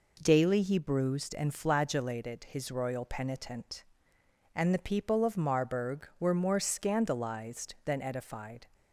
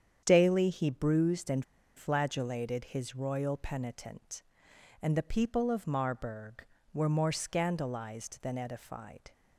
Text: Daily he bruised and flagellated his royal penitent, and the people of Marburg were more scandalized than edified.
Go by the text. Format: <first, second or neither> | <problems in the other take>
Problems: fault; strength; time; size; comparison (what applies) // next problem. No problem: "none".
first | starts louder than the rest; strong; until 1.2 s; 8.5 dB // pauses between "and" and "flagellated"; slight; at 1.6 s; 0.34 s long